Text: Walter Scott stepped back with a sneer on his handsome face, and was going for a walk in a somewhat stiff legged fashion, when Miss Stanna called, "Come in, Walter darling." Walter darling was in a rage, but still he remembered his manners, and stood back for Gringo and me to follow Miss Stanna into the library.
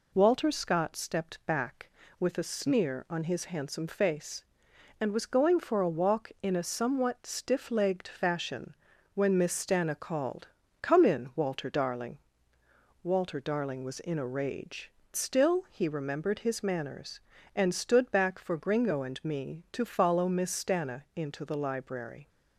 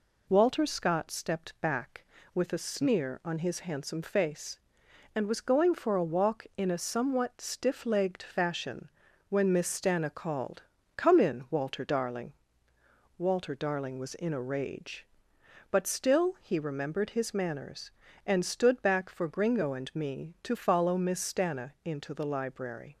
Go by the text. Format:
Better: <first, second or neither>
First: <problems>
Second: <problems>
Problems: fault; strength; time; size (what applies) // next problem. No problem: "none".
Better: second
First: skips "but"; at 15.0 s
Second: none